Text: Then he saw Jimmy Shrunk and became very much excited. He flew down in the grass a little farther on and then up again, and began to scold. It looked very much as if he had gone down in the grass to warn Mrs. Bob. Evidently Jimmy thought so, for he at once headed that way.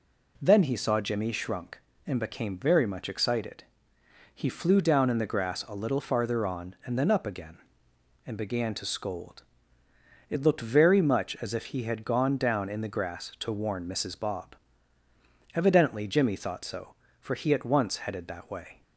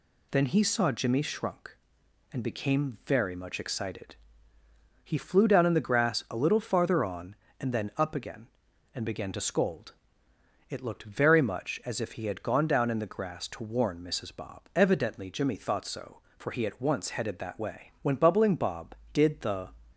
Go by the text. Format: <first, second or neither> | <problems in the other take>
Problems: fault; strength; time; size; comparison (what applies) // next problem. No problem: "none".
first | goes on to say "When Bubbling Bob did the"; strong; from 18.0 s on; 1.6 s long